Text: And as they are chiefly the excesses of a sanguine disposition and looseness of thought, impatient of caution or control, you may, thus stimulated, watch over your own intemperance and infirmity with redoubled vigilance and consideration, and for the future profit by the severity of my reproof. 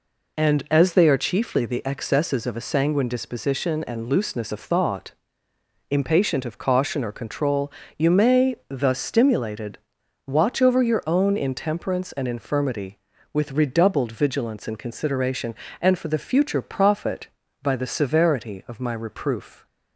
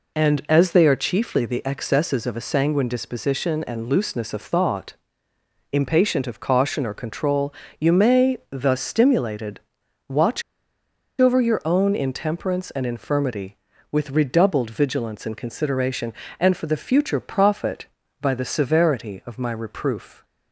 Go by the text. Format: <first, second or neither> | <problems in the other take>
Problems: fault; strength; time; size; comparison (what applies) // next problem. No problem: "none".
first | pauses between "watch" and "over"; noticeable; at 10.4 s; 0.78 s long